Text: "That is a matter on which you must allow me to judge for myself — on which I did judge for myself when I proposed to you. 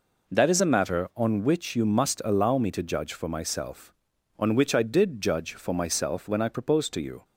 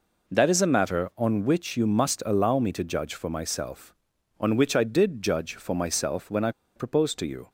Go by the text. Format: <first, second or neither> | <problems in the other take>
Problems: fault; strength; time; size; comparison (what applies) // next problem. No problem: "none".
first | pauses between "I" and "proposed"; slight; at 6.5 s; 0.24 s long